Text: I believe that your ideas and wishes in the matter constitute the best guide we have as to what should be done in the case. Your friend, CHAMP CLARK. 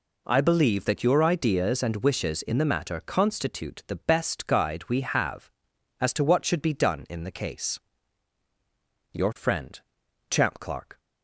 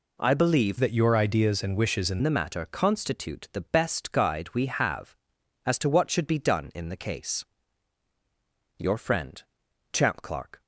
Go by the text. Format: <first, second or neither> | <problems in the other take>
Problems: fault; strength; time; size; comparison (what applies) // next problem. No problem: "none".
first | changes voice from "that" to "in"; from 0.7 to 2.1 s; 1.4 s long